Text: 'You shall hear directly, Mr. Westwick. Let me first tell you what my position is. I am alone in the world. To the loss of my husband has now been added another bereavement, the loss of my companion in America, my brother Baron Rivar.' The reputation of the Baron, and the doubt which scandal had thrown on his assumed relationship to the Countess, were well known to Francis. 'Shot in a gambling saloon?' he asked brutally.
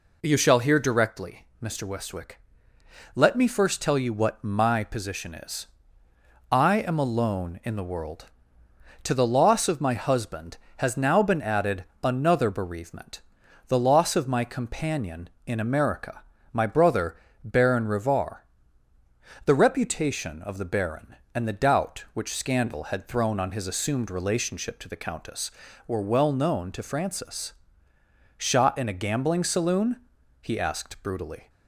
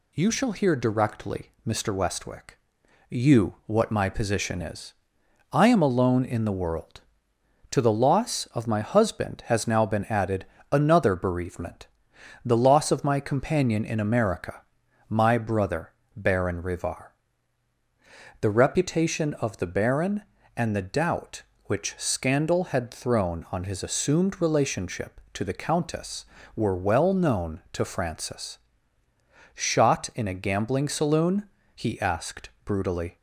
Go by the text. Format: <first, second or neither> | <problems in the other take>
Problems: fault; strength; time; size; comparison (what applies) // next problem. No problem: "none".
first | skips "Let me first tell"; at 2.8 s // pauses between "added" and "another"; slight; at 10.4 s; 0.26 s long; slight in the first // pauses between "brother" and "Baron"; slight; at 15.9 s; 0.22 s long; slight in the first